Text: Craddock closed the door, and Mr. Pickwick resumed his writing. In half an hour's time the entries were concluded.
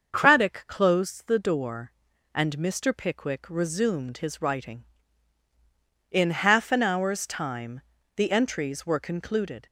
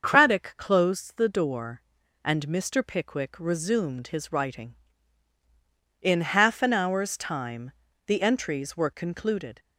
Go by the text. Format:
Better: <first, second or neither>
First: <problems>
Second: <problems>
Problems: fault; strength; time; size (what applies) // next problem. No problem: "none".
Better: neither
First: starts louder than the rest; until 1.2 s; 6.5 dB // pauses between "time" and "the"; slight; at 7.7 s; 0.34 s long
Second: starts louder than the rest; until 1.1 s; 6.5 dB // pauses between "time" and "the"; slight; at 7.7 s; 0.34 s long